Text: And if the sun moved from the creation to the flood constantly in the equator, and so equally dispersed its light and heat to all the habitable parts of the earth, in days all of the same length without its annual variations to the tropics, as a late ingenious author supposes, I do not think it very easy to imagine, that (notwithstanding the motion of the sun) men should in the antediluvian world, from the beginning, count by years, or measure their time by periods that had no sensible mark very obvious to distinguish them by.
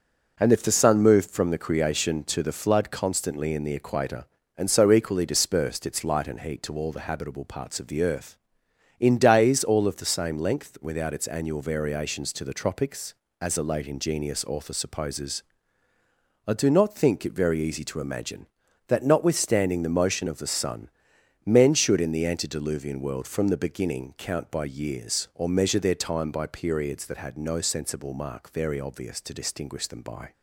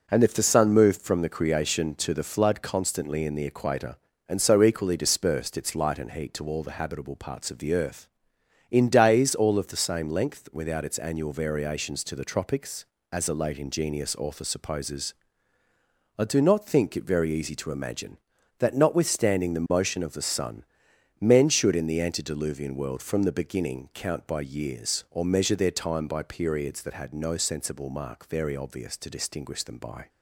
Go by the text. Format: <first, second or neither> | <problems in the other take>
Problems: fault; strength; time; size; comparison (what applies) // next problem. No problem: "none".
neither | none